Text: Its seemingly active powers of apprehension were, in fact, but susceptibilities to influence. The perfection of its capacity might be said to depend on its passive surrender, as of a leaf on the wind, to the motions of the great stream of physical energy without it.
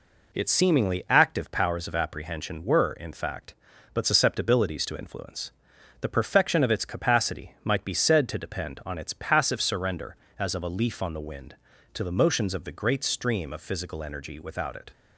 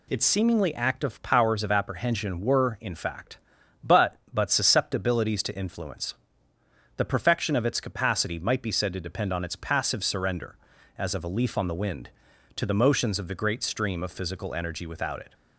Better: first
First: none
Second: says "but" twice; at 4.3 s

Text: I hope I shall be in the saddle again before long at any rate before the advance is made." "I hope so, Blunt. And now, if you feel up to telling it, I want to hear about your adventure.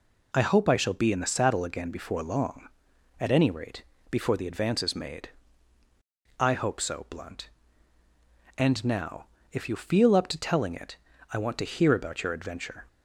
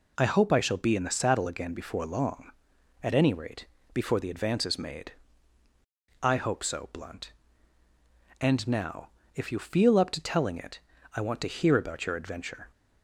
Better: neither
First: pauses between "rate" and "before"; slight; at 3.8 s; 0.28 s long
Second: pauses between "rate" and "before"; slight; at 3.6 s; 0.28 s long

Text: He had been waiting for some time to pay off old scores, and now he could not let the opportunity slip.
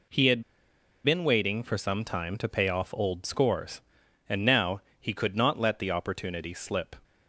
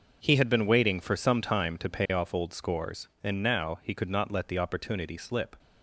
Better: second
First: pauses between "had" and "been"; noticeable; at 0.4 s; 0.61 s long // pauses between "now" and "he"; slight; at 4.8 s; 0.20 s long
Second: none

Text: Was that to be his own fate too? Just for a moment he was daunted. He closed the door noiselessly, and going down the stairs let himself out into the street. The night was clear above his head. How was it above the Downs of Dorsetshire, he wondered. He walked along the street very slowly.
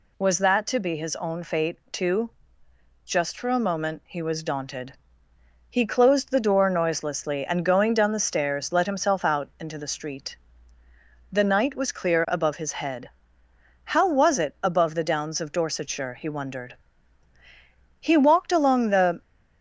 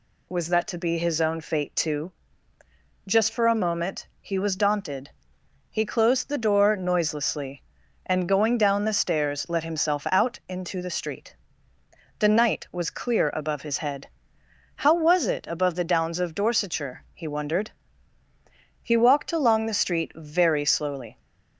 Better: second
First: pauses between "fate" and "too"; slight; at 1.7 s; 0.16 s long // stops before "street very slowly"; at 19.2 s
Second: none

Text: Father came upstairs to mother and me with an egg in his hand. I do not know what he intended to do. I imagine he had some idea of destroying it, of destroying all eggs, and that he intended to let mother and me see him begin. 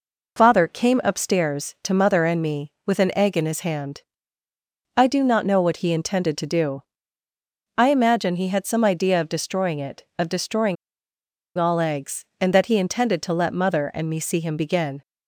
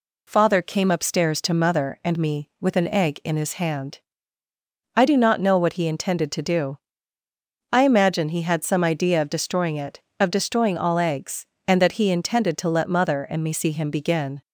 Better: second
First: pauses between "destroying" and "all"; noticeable; at 10.7 s; 0.81 s long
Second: none

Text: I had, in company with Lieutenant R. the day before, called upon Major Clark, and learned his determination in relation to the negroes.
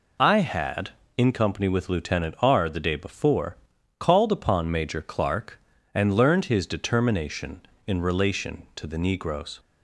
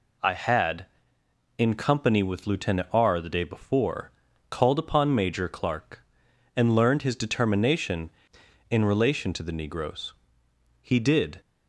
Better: first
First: none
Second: goes on to say "He did"; from 10.8 s on; 0.58 s long

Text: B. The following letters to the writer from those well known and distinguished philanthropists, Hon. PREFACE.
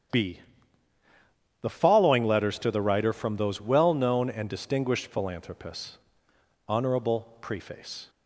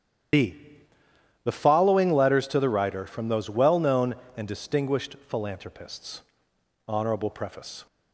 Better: first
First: starts louder than the rest; strong; until 2.3 s; 9.5 dB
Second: loses the start of "B"; at 0.3 s; 60 ms // starts louder than the rest; strong; until 2.2 s; 10.5 dB

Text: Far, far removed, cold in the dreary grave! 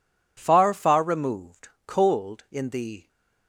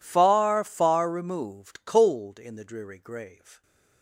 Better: second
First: stops before "dreary grave"; at 3.0 s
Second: none

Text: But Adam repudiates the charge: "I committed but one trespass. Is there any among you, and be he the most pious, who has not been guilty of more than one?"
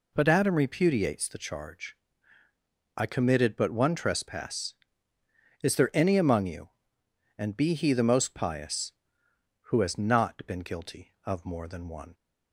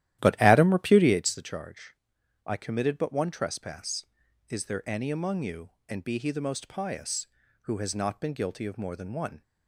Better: first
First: none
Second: starts louder than the rest; strong; until 1.2 s; 13 dB

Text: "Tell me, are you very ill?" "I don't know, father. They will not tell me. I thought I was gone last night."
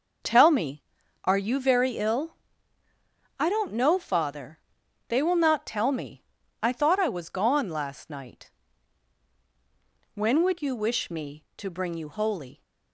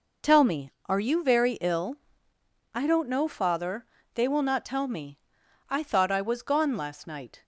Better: second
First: goes on to say "When would you wish me to bring you Holy"; strong; from 10.1 s on; 2.4 s long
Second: none

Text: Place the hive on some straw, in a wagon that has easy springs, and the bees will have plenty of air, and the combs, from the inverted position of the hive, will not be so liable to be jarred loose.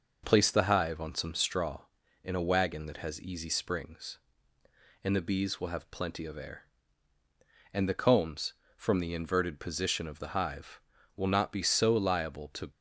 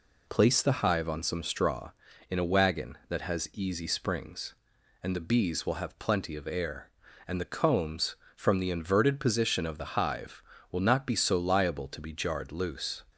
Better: second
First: stops before "be jarred loose"; at 12.7 s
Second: none

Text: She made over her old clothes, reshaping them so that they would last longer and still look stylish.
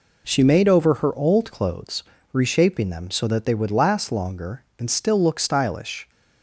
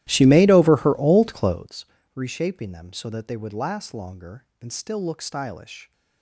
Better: first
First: none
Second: starts louder than the rest; strong; until 1.8 s; 14.5 dB

